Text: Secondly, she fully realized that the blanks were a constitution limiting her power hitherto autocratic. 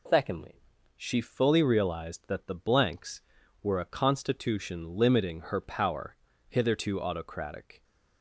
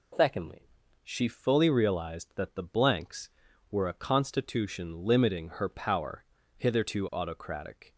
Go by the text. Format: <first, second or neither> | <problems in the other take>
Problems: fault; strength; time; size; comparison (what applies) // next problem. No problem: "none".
neither | pauses between "power" and "hitherto"; slight; the same in both